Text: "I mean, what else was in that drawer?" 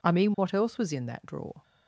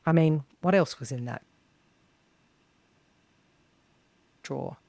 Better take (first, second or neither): first